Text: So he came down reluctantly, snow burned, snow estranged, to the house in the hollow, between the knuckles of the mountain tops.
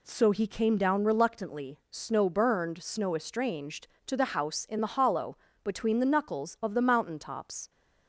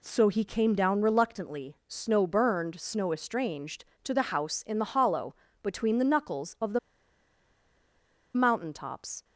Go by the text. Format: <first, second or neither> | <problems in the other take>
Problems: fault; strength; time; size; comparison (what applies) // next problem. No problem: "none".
first | pauses between "the" and "mountain"; strong; at 6.7 s; 1.5 s long